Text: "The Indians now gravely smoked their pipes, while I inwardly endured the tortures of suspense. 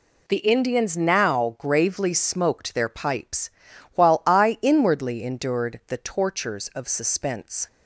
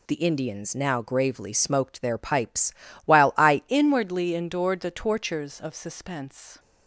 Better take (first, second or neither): first